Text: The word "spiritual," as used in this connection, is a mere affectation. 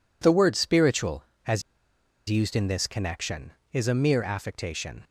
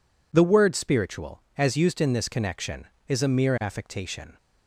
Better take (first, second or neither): second